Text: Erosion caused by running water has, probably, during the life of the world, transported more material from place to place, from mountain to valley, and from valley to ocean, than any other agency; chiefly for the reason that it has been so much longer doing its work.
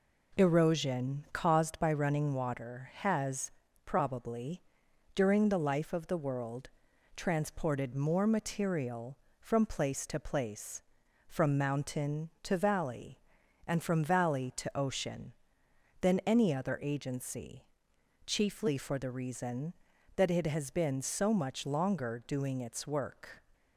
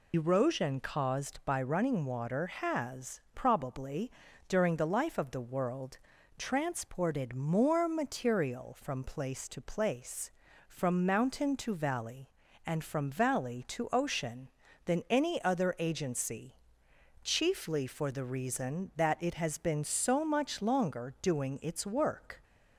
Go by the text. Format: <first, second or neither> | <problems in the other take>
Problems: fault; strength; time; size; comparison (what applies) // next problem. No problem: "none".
first | loses the start of "Erosion"; at 0.1 s; 70 ms